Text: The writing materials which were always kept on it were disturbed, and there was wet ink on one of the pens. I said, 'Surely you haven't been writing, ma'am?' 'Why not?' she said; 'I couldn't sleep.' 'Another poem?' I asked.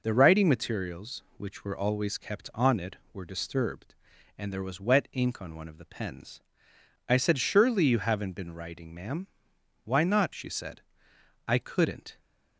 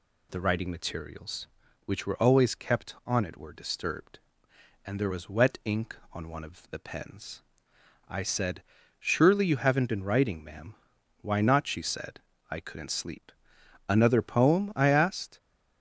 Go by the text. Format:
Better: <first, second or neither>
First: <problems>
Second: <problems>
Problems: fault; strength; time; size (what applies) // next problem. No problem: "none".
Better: second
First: stops before "sleep Another poem I asked"; at 12.1 s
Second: none